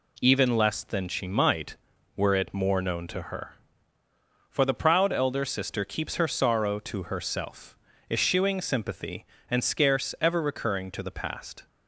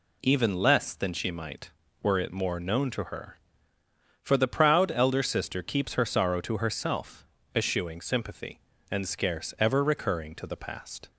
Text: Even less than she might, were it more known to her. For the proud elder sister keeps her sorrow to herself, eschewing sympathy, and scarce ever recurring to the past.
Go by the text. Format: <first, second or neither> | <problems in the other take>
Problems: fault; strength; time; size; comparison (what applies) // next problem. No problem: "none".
neither | none